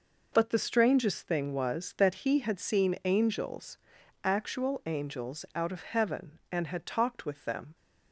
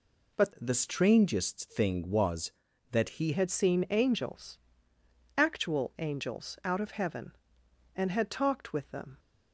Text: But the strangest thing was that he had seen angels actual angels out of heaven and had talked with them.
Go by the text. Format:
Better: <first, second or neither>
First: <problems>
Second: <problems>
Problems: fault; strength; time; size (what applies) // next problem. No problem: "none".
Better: first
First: pauses between "angels" and "actual"; noticeable; at 3.7 s; 0.48 s long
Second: changes voice from "the" to "he"; from 0.5 to 3.3 s; 2.8 s long // pauses between "angels" and "actual"; noticeable; at 4.5 s; 0.78 s long